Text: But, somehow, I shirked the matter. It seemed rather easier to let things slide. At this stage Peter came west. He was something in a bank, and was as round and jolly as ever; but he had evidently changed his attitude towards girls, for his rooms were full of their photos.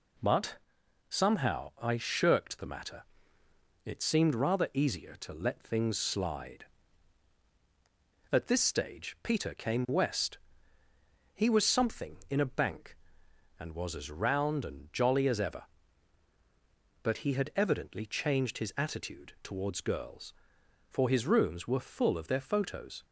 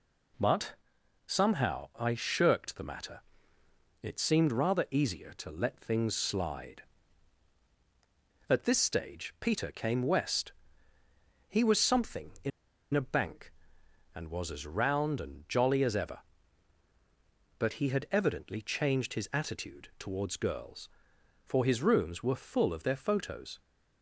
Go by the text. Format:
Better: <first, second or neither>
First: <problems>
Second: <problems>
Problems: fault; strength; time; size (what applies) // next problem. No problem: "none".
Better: first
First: none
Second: pauses between "in" and "a"; at 12.5 s; 0.44 s long